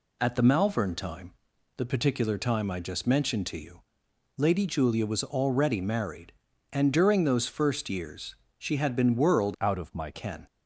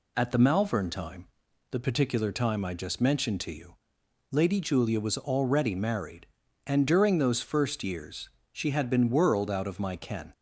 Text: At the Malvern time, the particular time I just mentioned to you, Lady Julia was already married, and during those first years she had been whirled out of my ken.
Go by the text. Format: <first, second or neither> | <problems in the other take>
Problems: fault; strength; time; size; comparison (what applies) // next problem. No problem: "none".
second | pauses between "years" and "she"; slight; at 8.3 s; 0.24 s long; slight in the second // changes voice from "out" to "my"; from 9.5 to 10.1 s; 0.6 s long